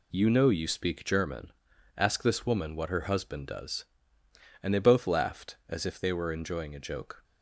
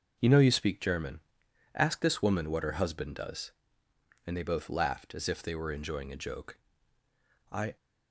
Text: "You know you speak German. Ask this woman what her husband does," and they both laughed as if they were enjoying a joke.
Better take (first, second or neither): first